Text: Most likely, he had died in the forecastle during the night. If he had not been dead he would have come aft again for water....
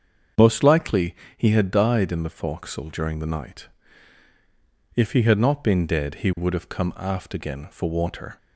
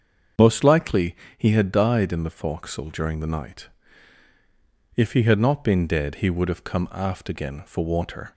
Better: neither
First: starts louder than the rest; until 1.6 s; 7 dB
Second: starts louder than the rest; until 1.6 s; 7 dB

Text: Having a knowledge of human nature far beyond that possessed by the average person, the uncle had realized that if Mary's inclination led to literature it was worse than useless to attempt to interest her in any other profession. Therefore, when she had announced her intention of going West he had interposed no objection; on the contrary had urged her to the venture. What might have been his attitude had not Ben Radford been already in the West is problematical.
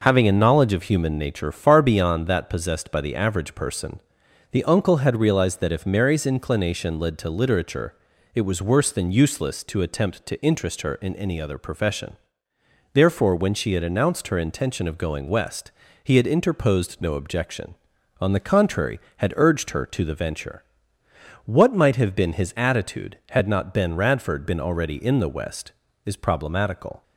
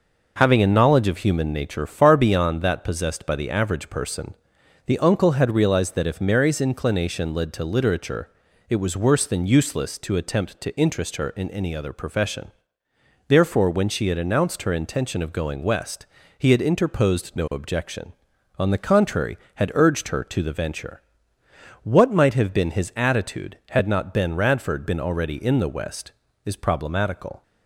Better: neither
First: pauses between "literature" and "it"; at 7.9 s; 0.40 s long // pauses between "West" and "he"; slight; at 15.7 s; 0.32 s long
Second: pauses between "literature" and "it"; at 8.2 s; 0.40 s long // pauses between "West" and "he"; slight; at 16.0 s; 0.32 s long

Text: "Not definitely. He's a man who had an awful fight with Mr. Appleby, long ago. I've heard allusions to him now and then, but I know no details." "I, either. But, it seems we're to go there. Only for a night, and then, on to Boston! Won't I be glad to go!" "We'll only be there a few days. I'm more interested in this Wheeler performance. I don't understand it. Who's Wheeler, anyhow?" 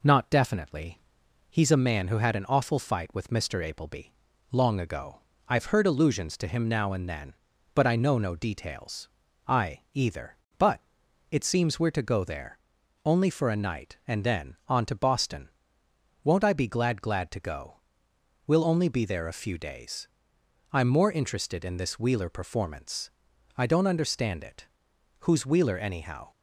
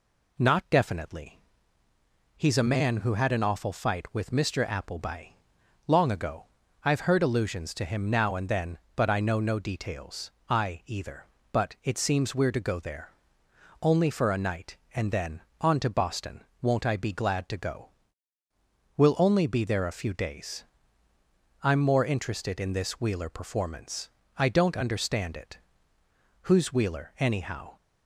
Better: second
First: says "glad" twice; at 17.0 s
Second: none

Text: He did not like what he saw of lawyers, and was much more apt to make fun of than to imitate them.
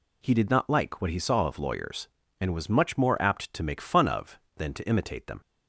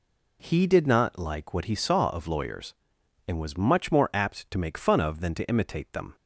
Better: neither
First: none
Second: none

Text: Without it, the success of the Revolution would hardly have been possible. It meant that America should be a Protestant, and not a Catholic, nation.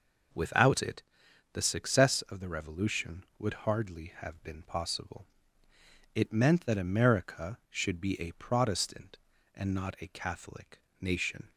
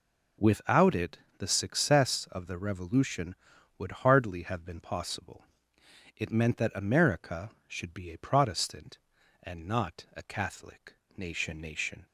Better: first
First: none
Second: says "nation" twice; at 11.5 s

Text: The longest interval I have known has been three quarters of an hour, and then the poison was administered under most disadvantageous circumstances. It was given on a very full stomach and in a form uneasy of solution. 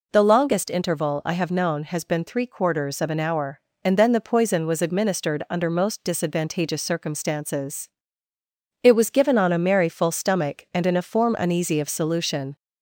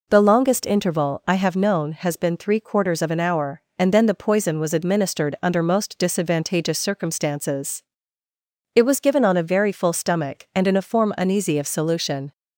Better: second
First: says "merry" for "very"; at 9.5 s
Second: none

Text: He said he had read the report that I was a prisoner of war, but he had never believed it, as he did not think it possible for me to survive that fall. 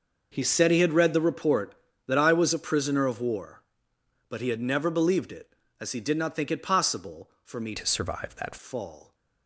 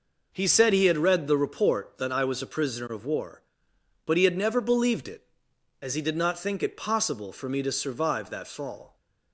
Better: second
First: changes voice from "to" to "that"; from 7.7 to 8.5 s; 0.8 s long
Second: none

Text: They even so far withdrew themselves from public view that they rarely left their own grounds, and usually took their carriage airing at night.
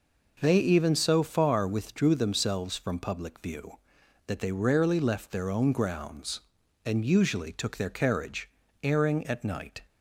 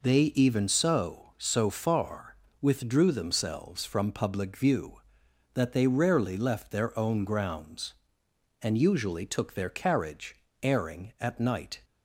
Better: first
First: pauses between "carriage" and "airing"; slight; at 8.4 s; 0.34 s long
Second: says "so" twice; at 1.3 s // pauses between "far" and "withdrew"; slight; at 2.3 s; 0.24 s long // pauses between "carriage" and "airing"; slight; at 10.3 s; 0.26 s long

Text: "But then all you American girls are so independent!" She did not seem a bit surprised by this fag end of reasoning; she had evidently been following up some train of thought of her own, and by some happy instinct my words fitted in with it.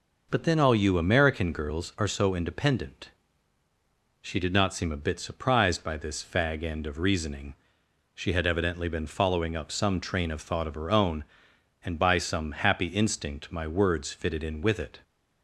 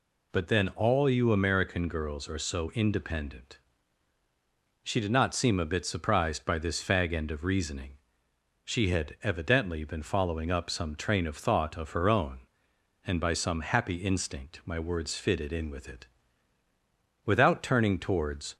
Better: first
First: none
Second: goes on to say "Without turning towards"; from 17.2 s on; 1.3 s long

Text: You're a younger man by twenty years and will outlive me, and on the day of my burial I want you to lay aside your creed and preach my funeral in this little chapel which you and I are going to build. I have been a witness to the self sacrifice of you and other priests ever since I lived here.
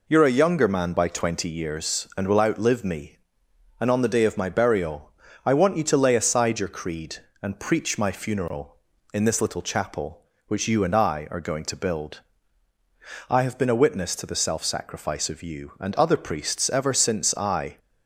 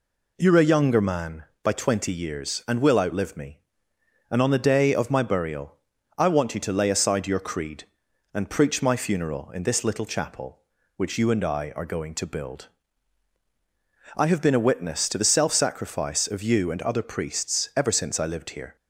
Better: second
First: pauses between "burial" and "I"; slight; at 5.1 s; 0.34 s long // stops before "lived here"; at 17.7 s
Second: pauses between "burial" and "I"; at 5.7 s; 0.42 s long

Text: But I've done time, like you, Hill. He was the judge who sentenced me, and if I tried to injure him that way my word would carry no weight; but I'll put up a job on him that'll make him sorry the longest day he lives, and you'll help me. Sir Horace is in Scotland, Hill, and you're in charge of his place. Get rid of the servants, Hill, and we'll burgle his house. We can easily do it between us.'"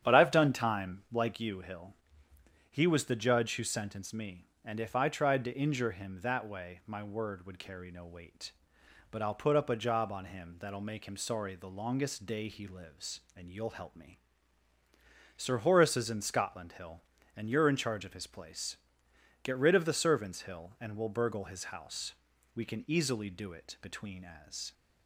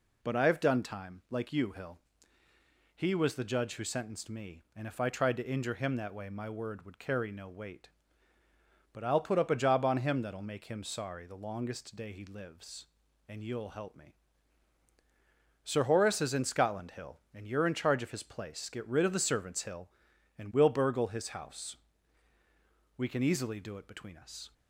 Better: second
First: starts louder than the rest; strong; until 1.0 s; 9.5 dB // says "as" for "us"; at 24.4 s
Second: none

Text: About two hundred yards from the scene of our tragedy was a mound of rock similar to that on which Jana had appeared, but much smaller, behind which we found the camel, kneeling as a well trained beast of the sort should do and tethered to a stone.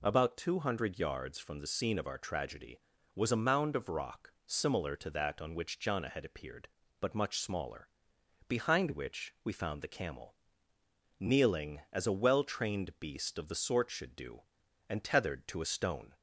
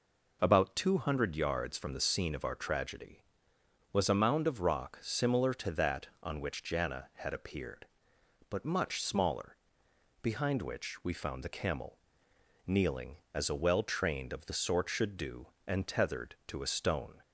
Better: first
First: none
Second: skips "beast"; at 14.3 s

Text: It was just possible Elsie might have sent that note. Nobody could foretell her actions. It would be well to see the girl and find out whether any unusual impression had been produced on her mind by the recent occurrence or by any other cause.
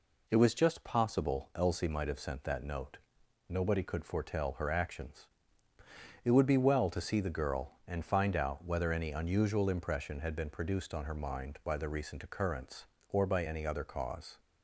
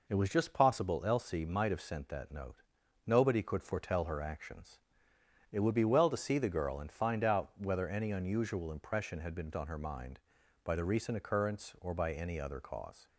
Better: first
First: none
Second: skips "produced"; at 9.5 s

